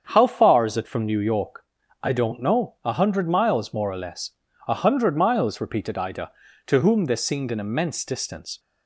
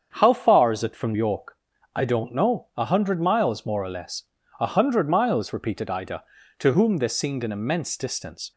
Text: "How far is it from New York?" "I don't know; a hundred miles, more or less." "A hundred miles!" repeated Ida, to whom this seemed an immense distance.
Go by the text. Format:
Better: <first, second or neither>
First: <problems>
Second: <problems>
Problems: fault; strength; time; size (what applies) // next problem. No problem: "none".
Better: first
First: starts louder than the rest; strong; until 1.1 s; 7.5 dB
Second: starts louder than the rest; strong; until 1.1 s; 7.5 dB // skips "New"; at 1.1 s